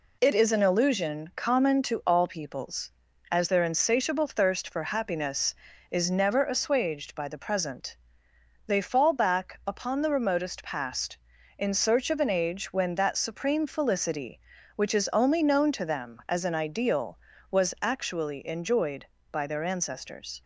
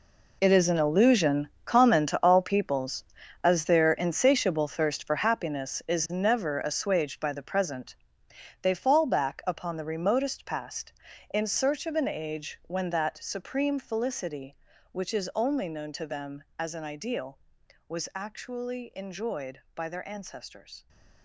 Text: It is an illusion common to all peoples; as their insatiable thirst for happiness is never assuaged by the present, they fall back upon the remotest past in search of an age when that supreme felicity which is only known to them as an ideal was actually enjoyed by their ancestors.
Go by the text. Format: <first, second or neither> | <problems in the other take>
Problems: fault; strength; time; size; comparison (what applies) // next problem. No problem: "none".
first | gets quieter; strong; throughout; 13 dB // pauses between "illusion" and "common"; slight; at 1.4 s; 0.16 s long